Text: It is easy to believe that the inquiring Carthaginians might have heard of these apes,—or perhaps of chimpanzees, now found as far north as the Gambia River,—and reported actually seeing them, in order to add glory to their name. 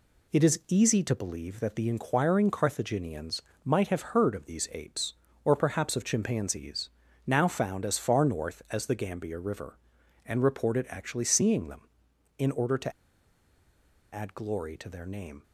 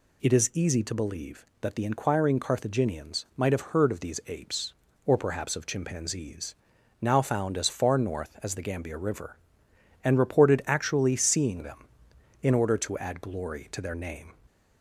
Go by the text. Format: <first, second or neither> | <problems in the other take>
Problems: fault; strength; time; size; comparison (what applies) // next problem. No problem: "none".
second | pauses between "Carthaginians" and "might"; slight; at 3.4 s; 0.24 s long // pauses between "to" and "add"; at 12.9 s; 1.2 s long